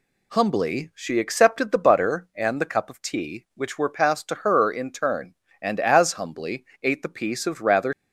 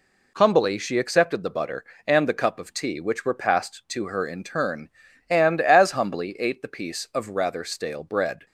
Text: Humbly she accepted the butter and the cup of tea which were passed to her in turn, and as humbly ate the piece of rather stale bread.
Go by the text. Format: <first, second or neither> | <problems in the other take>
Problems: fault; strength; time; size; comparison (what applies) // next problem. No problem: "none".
second | pauses between "humbly" and "ate"; slight; at 6.6 s; 0.18 s long // stops before "stale bread"; at 7.9 s